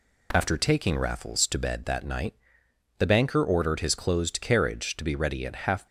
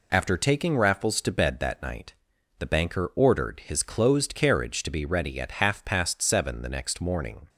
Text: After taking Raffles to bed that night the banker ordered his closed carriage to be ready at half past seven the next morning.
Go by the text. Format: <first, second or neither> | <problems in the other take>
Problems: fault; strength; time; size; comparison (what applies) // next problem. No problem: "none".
second | pauses between "night" and "the"; noticeable; at 2.3 s; 0.64 s long; also in the second // stops before "past seven the next morning"; at 5.8 s